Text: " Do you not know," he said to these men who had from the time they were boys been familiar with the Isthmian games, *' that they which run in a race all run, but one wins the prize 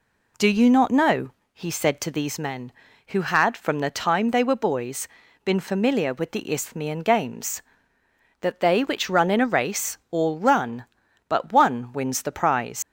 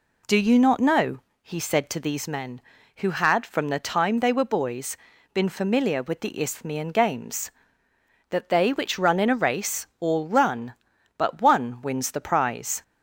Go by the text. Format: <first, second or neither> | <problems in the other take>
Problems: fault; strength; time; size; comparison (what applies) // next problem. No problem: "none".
second | pauses between "boys" and "been"; at 5.0 s; 0.38 s long; also in the second // leaves "prize" unfinished; at 12.8 s; 110 ms